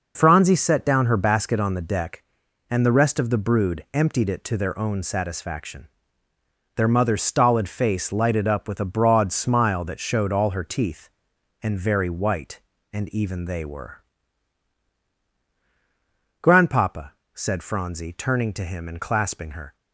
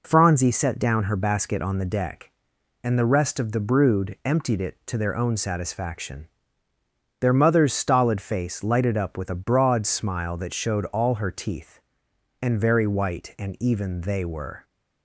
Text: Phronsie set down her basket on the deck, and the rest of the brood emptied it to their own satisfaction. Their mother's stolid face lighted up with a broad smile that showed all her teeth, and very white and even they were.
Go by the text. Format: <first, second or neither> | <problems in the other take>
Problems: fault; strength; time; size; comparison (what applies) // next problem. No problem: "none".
second | goes on to say "Grandpapa said Phronsie turning to him and clasping her"; strong; from 16.4 s on; 3.3 s long